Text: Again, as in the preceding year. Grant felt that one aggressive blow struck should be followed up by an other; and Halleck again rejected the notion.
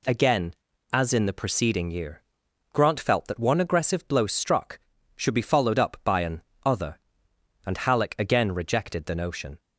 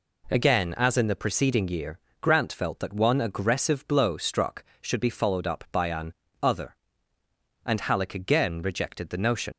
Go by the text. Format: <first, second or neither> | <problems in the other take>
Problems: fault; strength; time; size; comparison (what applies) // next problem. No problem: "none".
first | pauses between "an" and "other"; slight; at 6.1 s; 0.26 s long; slight in the first // leaves "notion" unfinished; at 9.5 s; 85 ms